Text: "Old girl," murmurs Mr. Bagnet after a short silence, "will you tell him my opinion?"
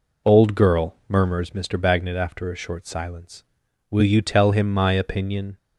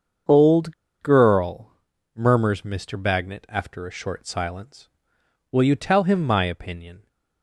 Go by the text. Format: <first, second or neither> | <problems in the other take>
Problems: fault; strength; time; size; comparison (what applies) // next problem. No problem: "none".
first | starts louder than the rest; until 1.5 s; 7 dB // pauses between "Old" and "girl"; slight; at 0.7 s; 0.27 s long